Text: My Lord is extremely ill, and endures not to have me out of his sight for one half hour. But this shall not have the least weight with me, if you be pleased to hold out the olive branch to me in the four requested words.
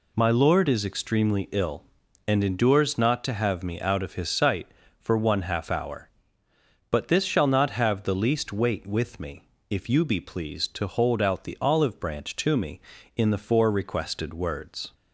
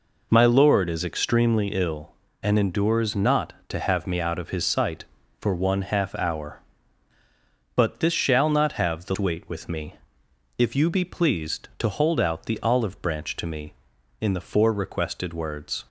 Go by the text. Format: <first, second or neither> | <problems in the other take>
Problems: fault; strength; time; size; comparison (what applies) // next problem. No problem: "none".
first | skips "least"; at 9.1 s